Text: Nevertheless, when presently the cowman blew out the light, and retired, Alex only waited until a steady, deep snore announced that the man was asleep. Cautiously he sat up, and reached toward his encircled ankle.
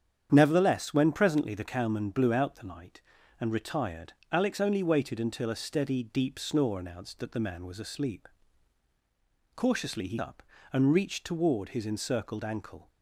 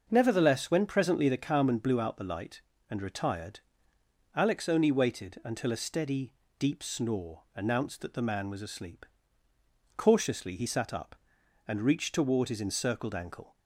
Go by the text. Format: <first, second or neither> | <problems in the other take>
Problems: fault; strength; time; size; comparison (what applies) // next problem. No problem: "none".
second | starts louder than the rest; strong; until 1.3 s; 8.5 dB; noticeable in the second // skips "sat"; at 10.1 s